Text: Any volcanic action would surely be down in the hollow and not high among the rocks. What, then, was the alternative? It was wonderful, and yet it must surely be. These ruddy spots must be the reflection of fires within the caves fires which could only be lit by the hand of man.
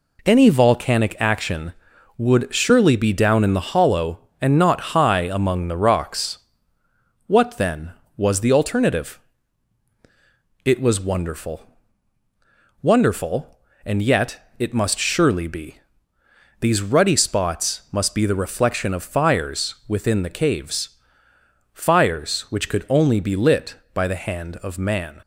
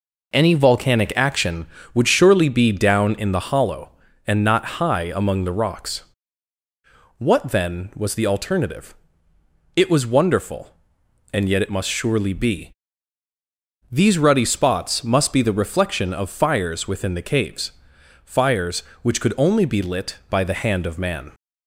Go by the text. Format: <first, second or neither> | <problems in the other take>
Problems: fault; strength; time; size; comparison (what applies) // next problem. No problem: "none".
second | says "wonderful" twice; at 12.8 s // pauses between "caves" and "fires"; noticeable; at 20.9 s; 0.78 s long; noticeable in the second